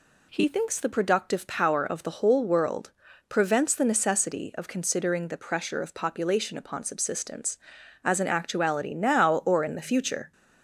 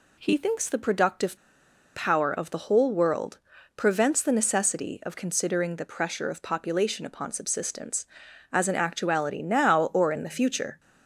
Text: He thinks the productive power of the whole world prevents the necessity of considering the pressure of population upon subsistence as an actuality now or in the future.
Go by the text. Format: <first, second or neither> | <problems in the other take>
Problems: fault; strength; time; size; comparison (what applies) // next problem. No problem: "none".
first | pauses between "productive" and "power"; noticeable; at 1.3 s; 0.58 s long // pauses between "world" and "prevents"; at 3.3 s; 0.40 s long; also in the first